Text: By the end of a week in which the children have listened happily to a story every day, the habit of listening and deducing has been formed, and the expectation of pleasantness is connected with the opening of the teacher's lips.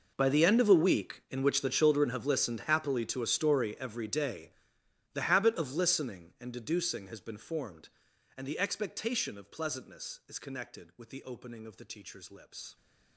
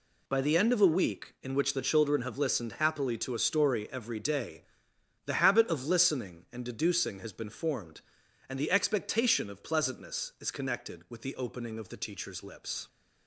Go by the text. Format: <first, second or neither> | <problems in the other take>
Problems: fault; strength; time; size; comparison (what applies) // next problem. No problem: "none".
second | gets quieter; strong; throughout; 19 dB